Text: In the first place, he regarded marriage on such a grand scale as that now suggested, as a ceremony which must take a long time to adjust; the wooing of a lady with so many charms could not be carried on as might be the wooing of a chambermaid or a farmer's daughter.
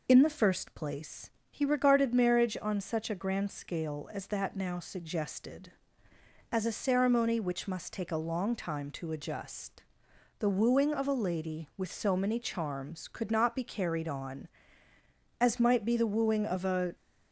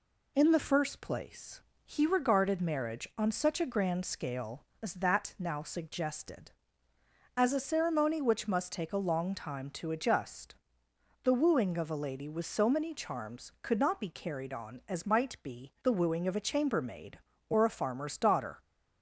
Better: second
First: stops before "chambermaid or a farmer's daughter"; at 16.9 s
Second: none

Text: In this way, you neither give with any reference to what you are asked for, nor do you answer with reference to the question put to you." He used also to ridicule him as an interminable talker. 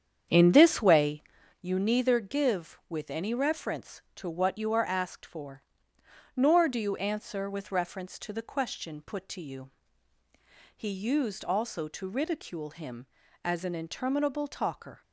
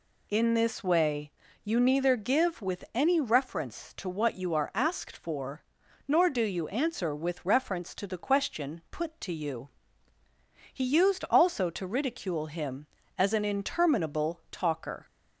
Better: second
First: starts louder than the rest; strong; until 1.6 s; 8 dB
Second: none

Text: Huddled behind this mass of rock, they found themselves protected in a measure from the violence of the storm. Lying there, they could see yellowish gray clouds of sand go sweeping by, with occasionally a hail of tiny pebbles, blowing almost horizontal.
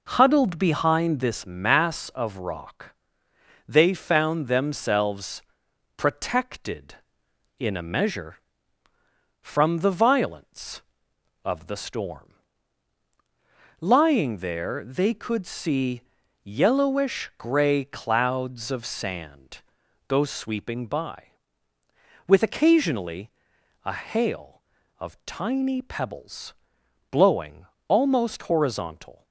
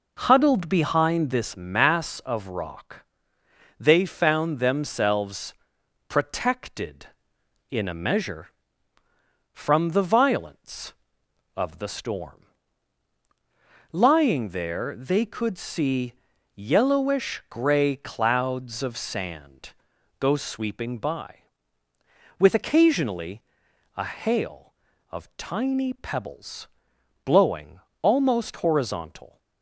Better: neither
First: pauses between "themselves" and "protected"; noticeable; at 5.4 s; 0.54 s long // pauses between "see" and "yellowish"; at 16.0 s; 0.42 s long // pauses between "sand" and "go"; at 19.6 s; 0.44 s long // pauses between "occasionally" and "a"; noticeable; at 23.3 s; 0.54 s long // pauses between "blowing" and "almost"; slight; at 27.6 s; 0.22 s long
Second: pauses between "themselves" and "protected"; noticeable; at 5.5 s; 0.54 s long // pauses between "see" and "yellowish"; at 16.1 s; 0.42 s long // pauses between "sand" and "go"; at 19.7 s; 0.44 s long // pauses between "occasionally" and "a"; noticeable; at 23.4 s; 0.54 s long // pauses between "blowing" and "almost"; slight; at 27.7 s; 0.22 s long

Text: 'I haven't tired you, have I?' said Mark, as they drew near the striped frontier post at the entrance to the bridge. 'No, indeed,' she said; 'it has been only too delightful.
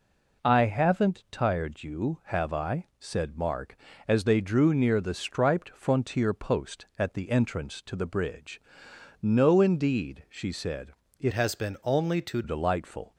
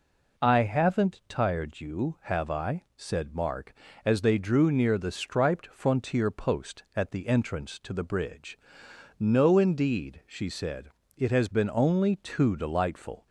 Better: second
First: changes voice from "has" to "too"; from 11.3 to 12.4 s; 1.1 s long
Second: none

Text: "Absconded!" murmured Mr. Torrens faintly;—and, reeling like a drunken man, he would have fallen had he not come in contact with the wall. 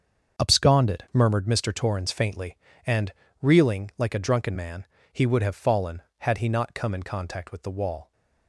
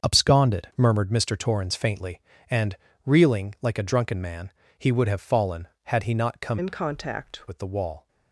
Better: first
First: starts louder than the rest; until 1.4 s; 7 dB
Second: starts louder than the rest; until 1.1 s; 7 dB // changes voice from "in" to "contact"; from 6.5 to 7.4 s; 0.9 s long

